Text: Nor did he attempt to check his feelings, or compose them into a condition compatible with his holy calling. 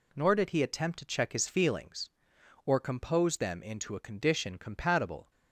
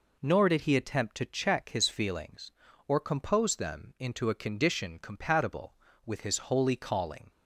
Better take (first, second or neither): second